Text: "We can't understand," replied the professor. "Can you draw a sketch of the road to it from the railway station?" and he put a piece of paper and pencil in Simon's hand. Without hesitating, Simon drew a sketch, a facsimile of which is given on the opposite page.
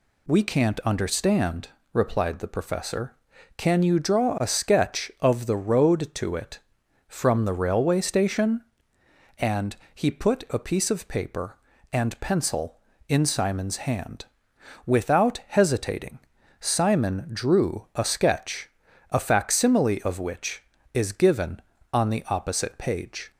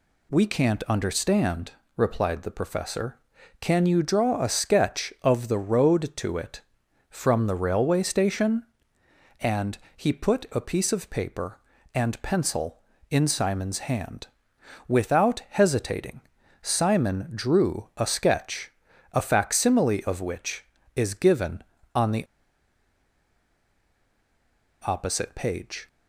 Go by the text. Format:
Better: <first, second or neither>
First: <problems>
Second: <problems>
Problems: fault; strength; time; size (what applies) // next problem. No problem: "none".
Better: first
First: pauses between "and" and "he"; slight; at 9.7 s; 0.18 s long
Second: pauses between "and" and "he"; slight; at 9.7 s; 0.18 s long // pauses between "the" and "opposite"; strong; at 22.2 s; 2.5 s long